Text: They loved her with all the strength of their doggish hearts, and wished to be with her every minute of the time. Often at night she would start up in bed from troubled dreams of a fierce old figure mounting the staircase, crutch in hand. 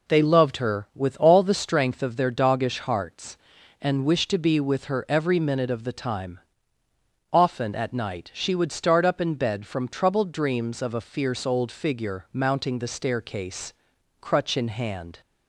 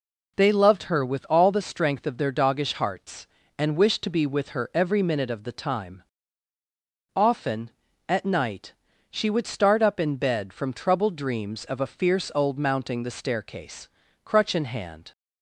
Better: first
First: none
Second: pauses between "night" and "she"; at 8.7 s; 0.38 s long // skips "figure"; at 12.5 s

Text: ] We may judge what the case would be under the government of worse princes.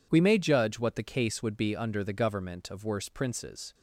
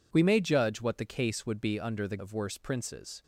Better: first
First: none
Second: skips "government"; at 2.1 s

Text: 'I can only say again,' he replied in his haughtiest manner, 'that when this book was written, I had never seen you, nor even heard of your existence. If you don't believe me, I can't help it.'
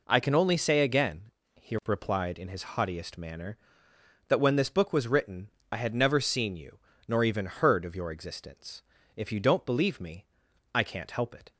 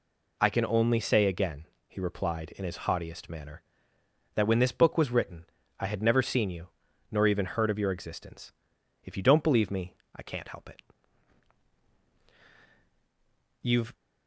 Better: first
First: none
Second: goes on to say "You've"; slight; from 13.6 s on; 0.32 s long

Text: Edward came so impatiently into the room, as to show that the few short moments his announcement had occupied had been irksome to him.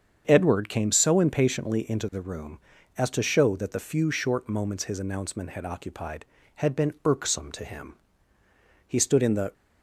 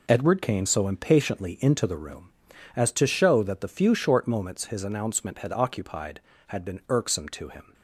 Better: second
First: starts louder than the rest; strong; until 1.2 s; 7.5 dB // goes on to say "He stood in the"; noticeable; from 8.8 s on; 0.64 s long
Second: none

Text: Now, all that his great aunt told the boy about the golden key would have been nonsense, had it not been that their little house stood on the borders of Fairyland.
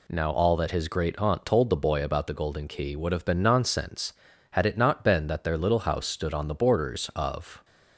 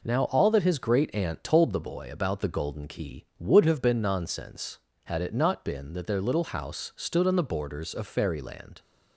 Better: second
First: stops before "Fairyland"; at 7.6 s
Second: none

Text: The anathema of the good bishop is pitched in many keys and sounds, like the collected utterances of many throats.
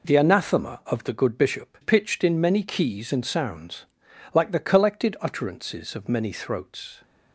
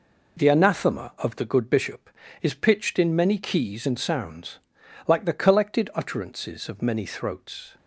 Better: second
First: skips "is"; at 1.7 s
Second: none

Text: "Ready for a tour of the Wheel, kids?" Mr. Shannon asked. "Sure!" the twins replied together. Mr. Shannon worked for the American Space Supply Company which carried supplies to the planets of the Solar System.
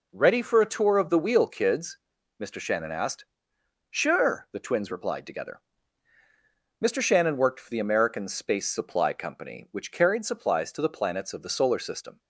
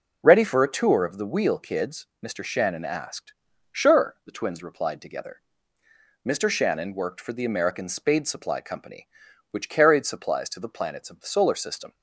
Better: first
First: none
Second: says "Spade" for "Space"; at 7.8 s

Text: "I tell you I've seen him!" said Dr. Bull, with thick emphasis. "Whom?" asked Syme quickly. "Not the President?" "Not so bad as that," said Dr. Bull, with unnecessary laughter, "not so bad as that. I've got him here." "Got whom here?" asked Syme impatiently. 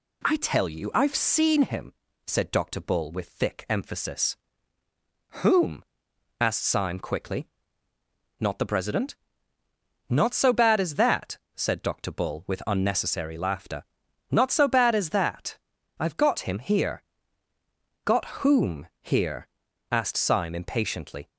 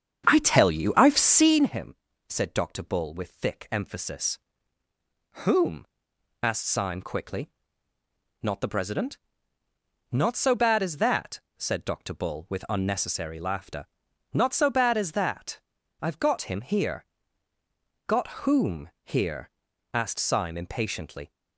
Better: first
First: pauses between "Got" and "whom"; slight; at 18.2 s; 0.18 s long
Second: starts louder than the rest; strong; until 1.7 s; 8 dB // pauses between "Got" and "whom"; slight; at 18.2 s; 0.18 s long

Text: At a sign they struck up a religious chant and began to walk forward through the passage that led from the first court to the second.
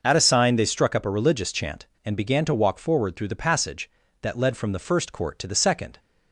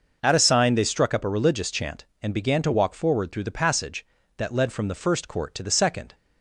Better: neither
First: none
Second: none

